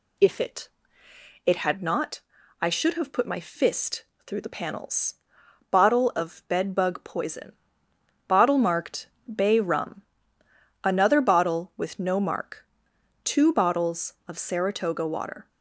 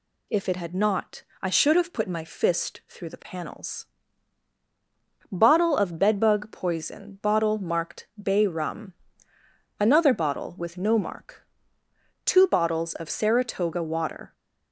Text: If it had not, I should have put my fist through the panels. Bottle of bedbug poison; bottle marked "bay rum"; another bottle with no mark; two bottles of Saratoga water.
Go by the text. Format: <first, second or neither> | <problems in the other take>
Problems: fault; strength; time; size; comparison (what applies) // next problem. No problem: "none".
second | says "it" twice; at 1.4 s // pauses between "fist" and "through"; slight; at 4.0 s; 0.22 s long // pauses between "marked" and "bay"; slight; at 9.0 s; 0.20 s long